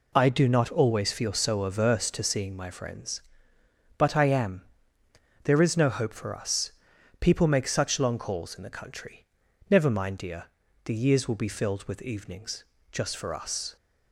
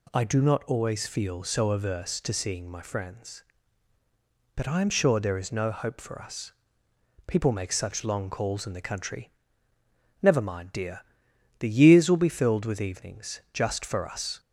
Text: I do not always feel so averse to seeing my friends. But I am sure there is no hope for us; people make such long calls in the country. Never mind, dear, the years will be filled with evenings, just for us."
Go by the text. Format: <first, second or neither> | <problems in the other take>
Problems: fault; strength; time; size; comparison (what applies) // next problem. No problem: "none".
second | skips "sure"; at 5.0 s